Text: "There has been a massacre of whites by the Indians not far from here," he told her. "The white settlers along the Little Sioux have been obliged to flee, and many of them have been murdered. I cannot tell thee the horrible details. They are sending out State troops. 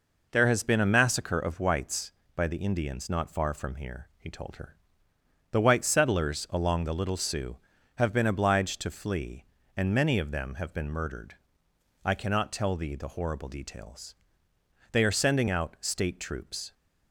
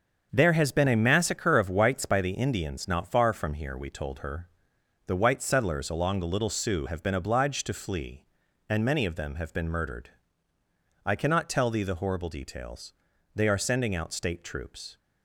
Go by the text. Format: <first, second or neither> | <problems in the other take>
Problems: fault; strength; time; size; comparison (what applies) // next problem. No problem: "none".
first | starts louder than the rest; until 1.3 s; 7 dB // says "we" for "he"; at 3.7 s